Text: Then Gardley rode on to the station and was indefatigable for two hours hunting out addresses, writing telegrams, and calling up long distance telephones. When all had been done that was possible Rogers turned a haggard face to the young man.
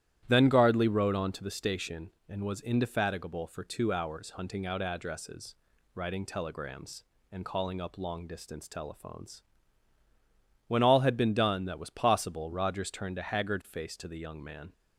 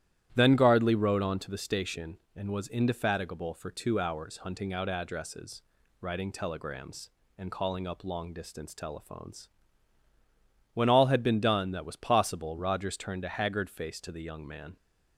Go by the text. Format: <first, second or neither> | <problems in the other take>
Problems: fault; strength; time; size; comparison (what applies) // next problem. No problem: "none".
neither | starts louder than the rest; strong; the same in both